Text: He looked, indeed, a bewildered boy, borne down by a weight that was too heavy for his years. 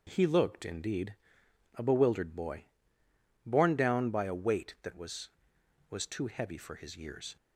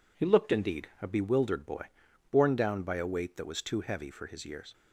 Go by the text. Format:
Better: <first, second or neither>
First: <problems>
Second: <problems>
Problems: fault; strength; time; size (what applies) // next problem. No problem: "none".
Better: second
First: starts louder than the rest; noticeable; until 1.0 s; 6 dB // says "was" twice; at 5.8 s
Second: none